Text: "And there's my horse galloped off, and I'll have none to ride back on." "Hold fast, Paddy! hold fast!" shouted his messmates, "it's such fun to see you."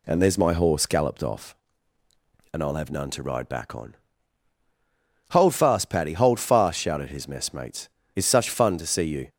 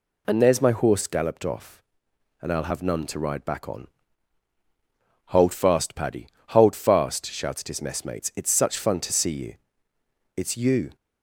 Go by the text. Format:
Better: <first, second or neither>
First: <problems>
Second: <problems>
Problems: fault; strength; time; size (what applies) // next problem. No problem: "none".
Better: first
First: none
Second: goes on to say "It's you"; from 10.3 s on; 0.60 s long